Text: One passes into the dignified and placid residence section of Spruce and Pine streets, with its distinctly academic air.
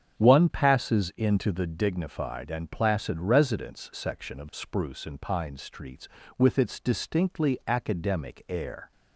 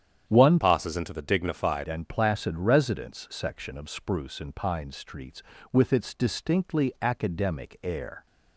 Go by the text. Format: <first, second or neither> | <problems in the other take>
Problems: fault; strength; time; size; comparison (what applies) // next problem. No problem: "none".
first | starts louder than the rest; strong; until 1.3 s; 9 dB; strong in the first // changes voice from "passes" to "dignified"; from 0.6 to 1.8 s; 1.2 s long